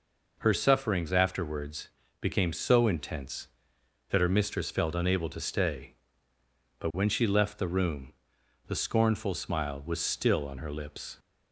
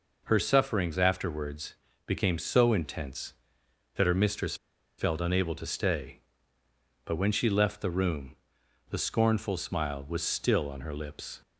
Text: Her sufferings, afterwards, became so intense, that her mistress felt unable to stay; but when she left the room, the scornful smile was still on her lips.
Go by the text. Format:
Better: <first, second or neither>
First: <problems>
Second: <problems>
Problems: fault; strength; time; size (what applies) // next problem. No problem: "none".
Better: first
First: none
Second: pauses between "mistress" and "felt"; at 4.5 s; 0.42 s long